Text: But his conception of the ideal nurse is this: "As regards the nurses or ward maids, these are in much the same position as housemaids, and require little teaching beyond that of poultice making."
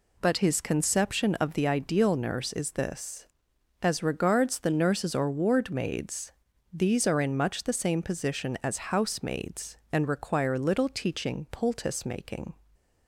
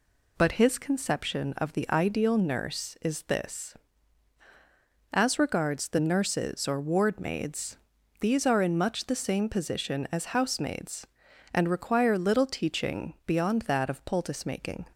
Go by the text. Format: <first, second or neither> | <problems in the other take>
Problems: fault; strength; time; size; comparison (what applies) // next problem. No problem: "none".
second | skips "beyond that of"; at 11.4 s